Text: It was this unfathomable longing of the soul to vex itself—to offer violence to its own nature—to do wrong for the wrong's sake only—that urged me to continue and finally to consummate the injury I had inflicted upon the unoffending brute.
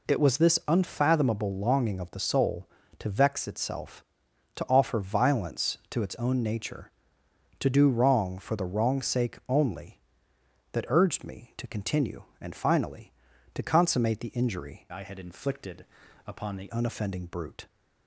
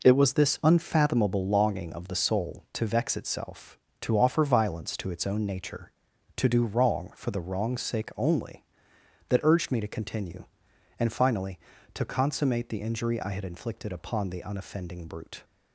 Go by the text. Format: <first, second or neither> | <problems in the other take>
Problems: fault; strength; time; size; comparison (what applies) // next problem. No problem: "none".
second | changes voice from "I" to "the"; from 14.9 to 16.6 s; 1.7 s long // pauses between "inflicted" and "upon"; at 15.8 s; 0.42 s long